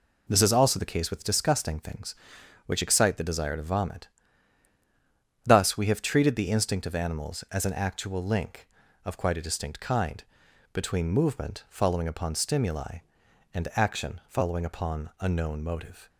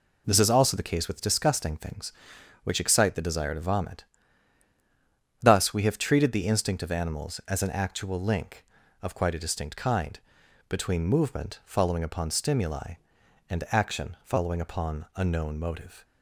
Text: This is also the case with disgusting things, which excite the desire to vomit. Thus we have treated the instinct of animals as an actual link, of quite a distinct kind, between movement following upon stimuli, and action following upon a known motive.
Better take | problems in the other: neither | none

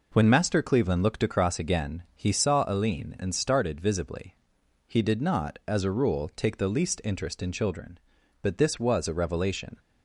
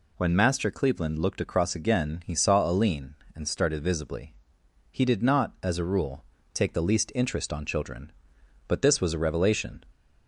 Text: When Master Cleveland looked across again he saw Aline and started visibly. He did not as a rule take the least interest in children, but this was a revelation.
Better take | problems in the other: first | pauses between "rule" and "take"; slight; at 6.2 s; 0.30 s long // says "on" for "in"; at 7.5 s

